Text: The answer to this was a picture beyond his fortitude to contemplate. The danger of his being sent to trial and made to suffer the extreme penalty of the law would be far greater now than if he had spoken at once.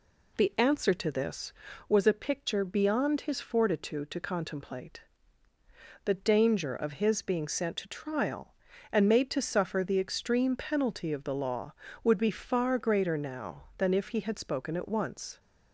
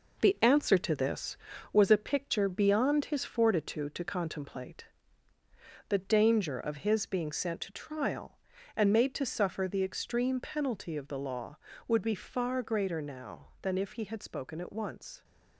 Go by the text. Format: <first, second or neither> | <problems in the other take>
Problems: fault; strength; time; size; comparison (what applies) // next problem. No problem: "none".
first | gets quieter; noticeable; throughout; 5.5 dB